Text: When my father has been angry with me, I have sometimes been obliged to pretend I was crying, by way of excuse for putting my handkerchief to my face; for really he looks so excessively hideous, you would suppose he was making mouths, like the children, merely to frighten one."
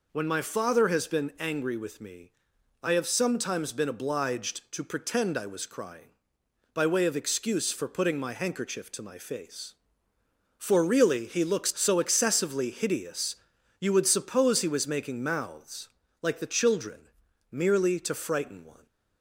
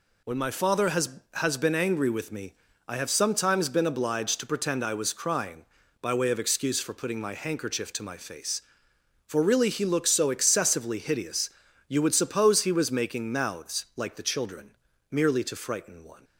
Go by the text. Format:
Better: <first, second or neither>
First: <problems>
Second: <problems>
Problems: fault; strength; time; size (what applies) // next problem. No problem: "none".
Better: first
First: none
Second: says "has" twice; at 1.3 s